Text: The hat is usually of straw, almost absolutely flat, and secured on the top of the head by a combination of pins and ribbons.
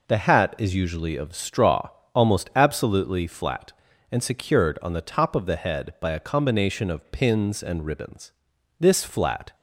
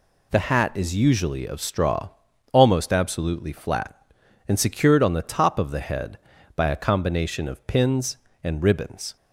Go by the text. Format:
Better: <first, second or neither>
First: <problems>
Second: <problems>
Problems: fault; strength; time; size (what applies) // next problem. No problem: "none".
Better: second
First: goes on to say "This flat"; noticeable; from 8.7 s on; 0.76 s long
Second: none